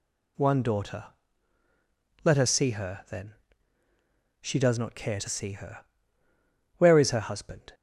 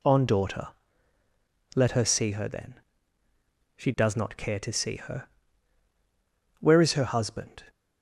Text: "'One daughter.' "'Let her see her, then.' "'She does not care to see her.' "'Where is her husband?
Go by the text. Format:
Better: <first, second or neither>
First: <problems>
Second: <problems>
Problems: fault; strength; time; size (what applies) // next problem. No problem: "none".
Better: first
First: none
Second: says "On" for "One"; at 0.0 s